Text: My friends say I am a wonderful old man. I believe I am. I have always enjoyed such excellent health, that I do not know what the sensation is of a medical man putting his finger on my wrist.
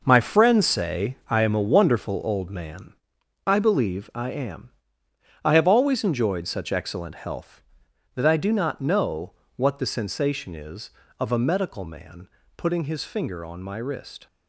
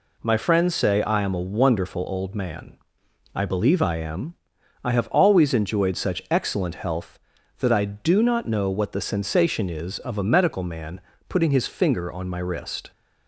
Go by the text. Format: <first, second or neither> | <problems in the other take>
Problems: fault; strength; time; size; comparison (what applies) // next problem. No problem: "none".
second | gets quieter; strong; throughout; 9.5 dB // pauses between "say" and "I"; slight; at 1.1 s; 0.16 s long // pauses between "know" and "what"; slight; at 9.3 s; 0.24 s long // pauses between "man" and "putting"; slight; at 12.2 s; 0.28 s long; slight in the second